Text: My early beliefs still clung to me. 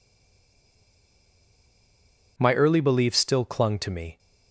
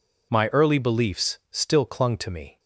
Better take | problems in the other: second | stays silent before the first word; until 2.3 s; 2.3 s long

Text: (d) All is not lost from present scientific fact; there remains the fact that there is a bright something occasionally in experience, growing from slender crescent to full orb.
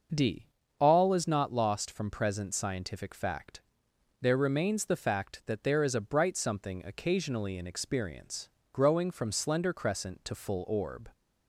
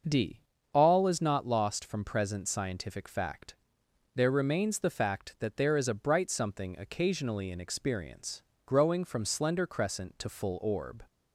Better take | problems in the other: neither | starts louder than the rest; the same in both

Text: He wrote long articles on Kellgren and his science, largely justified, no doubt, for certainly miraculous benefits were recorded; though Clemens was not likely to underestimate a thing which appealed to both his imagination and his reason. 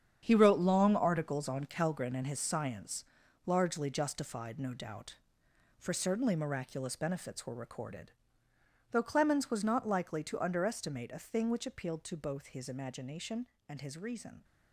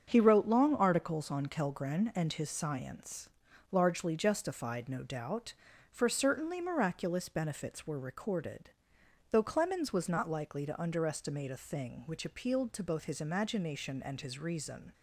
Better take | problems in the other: second | gets quieter; strong; throughout; 10.5 dB // starts louder than the rest; strong; until 1.2 s; 8 dB; strong in the second

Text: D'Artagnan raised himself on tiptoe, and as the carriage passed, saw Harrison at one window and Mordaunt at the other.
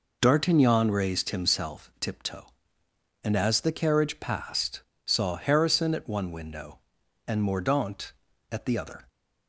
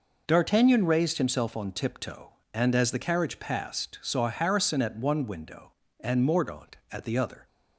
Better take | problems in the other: second | skips "on"; at 1.9 s

